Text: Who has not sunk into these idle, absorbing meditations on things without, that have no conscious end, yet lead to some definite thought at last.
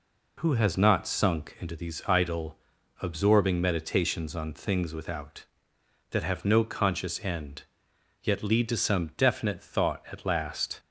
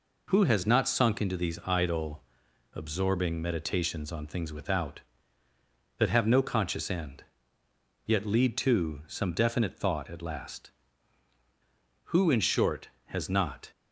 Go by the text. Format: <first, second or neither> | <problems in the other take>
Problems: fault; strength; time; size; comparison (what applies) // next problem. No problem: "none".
first | goes on to say "Who in short has not"; from 12.1 s on; 1.5 s long